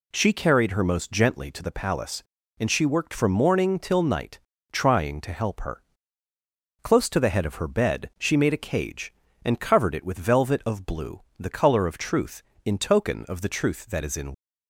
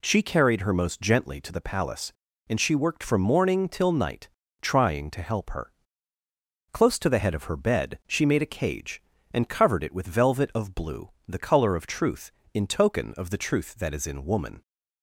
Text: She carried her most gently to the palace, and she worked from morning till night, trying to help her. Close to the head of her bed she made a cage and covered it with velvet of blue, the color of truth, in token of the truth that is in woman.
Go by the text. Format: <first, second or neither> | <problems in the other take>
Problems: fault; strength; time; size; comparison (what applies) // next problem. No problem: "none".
second | stops before "woman"; at 14.3 s